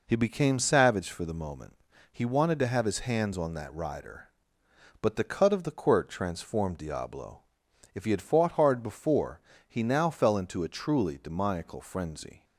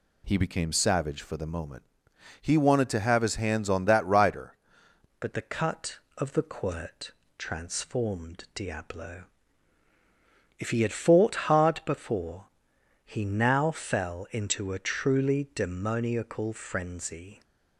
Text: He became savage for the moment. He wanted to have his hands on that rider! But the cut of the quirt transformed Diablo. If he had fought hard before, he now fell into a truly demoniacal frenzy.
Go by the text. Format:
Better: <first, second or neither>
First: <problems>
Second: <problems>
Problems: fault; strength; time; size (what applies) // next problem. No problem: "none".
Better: first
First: none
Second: changes voice at "But"; from 5.1 s on; 12.3 s long // pauses between "quirt" and "transformed"; slight; at 7.1 s; 0.26 s long